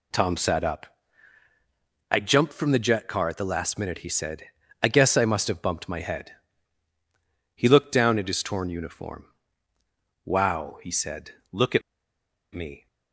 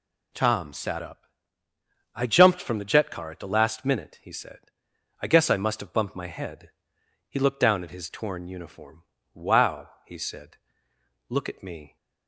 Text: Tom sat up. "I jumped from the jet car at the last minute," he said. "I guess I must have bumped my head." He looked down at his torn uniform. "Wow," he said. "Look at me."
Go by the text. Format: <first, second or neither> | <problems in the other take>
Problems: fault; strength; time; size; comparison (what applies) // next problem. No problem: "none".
second | pauses between "at" and "me"; noticeable; at 11.8 s; 0.73 s long